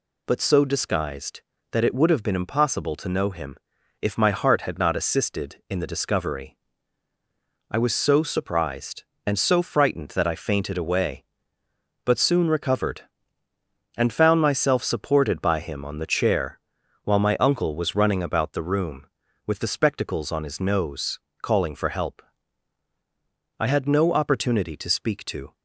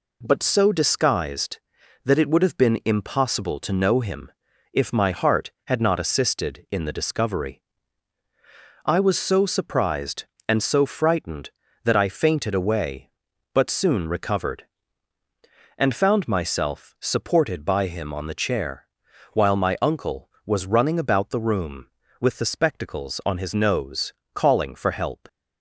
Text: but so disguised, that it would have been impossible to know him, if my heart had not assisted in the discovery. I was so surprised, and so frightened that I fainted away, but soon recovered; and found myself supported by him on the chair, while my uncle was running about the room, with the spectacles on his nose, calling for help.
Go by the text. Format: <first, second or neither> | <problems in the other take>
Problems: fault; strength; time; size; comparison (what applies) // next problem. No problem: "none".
second | goes on to say "I had no opportunity to speak to"; strong; from 23.5 s on; 1.9 s long